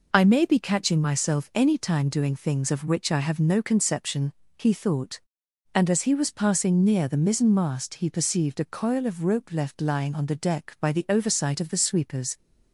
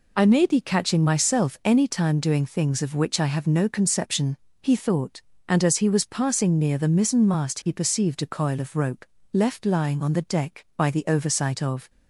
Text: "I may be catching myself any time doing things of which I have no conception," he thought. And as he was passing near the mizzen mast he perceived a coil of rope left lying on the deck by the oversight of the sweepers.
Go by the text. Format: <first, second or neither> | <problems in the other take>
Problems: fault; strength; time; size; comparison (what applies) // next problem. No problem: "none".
first | pauses between "rope" and "left"; slight; at 9.0 s; 0.26 s long // stops before "the sweepers"; at 11.8 s